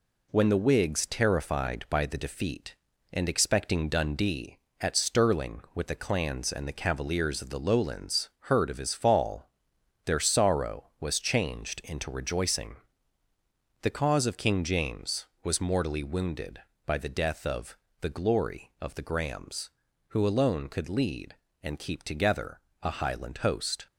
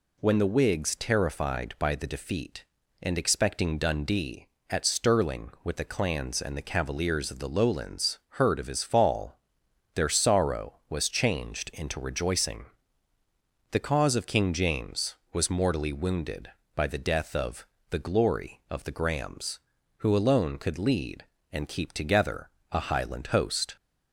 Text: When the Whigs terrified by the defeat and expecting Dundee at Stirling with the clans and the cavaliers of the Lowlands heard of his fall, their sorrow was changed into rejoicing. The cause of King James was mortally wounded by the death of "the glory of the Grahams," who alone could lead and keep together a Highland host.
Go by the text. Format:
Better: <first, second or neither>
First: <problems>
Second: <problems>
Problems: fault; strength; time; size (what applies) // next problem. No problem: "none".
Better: second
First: gets quieter; noticeable; throughout; 4 dB // pauses between "of" and "the"; slight; at 17.7 s; 0.24 s long // pauses between "together" and "a"; slight; at 22.6 s; 0.22 s long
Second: pauses between "of" and "the"; slight; at 17.6 s; 0.24 s long // pauses between "together" and "a"; slight; at 22.4 s; 0.22 s long